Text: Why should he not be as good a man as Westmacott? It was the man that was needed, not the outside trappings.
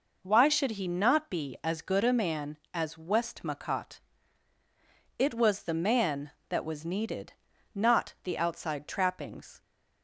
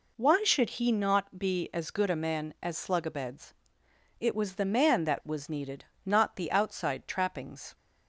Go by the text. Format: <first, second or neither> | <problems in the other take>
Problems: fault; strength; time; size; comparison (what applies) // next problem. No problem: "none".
first | says "Slugabeds" for "Westmacott"; at 2.7 s